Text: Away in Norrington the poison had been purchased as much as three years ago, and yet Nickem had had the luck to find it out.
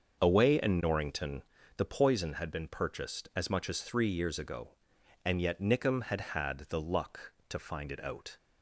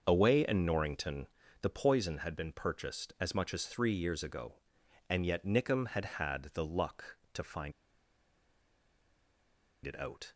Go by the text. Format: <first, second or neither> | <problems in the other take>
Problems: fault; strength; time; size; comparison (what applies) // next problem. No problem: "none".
first | starts louder than the rest; until 1.0 s; 6.5 dB; also in the first // pauses between "Norrington" and "the"; slight; at 1.2 s; 0.34 s long; slight in the first // pauses between "find" and "it"; strong; at 7.7 s; 2.1 s long